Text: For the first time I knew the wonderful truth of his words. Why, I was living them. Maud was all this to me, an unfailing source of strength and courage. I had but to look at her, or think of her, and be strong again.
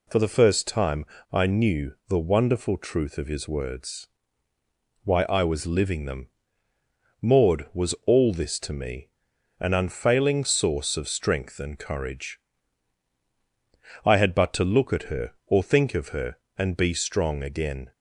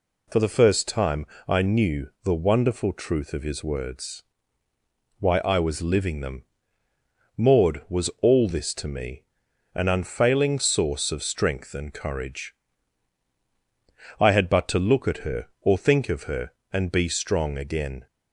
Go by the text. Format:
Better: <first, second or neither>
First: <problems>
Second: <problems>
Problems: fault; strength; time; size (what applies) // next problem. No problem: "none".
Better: neither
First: pauses between "time" and "I"; slight; at 1.0 s; 0.27 s long // pauses between "knew" and "the"; slight; at 1.9 s; 0.16 s long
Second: pauses between "time" and "I"; slight; at 1.2 s; 0.22 s long // pauses between "knew" and "the"; slight; at 2.0 s; 0.16 s long